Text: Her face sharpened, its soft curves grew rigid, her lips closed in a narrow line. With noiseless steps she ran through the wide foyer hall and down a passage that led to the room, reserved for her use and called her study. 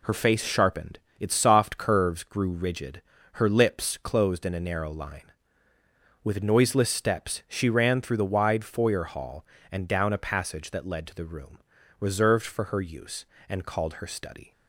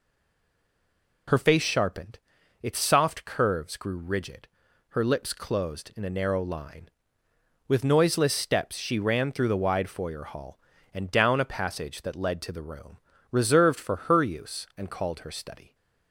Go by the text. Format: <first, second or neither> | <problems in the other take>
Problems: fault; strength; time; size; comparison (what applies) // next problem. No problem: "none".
first | stays silent before the first word; noticeable; until 1.2 s; 1.2 s long